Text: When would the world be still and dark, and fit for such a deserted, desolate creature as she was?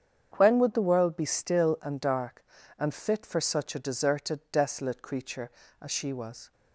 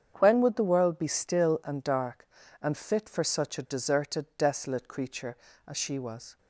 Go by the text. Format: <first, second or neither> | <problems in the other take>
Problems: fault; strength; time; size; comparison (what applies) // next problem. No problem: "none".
neither | starts louder than the rest; strong; the same in both